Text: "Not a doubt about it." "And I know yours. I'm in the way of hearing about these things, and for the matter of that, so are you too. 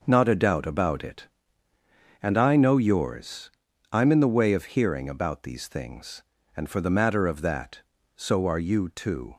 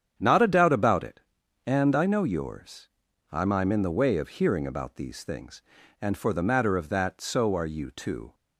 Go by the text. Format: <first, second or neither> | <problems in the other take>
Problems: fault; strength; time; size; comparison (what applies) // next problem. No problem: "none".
first | starts louder than the rest; strong; until 1.1 s; 8.5 dB // says "I'm" twice; at 3.5 s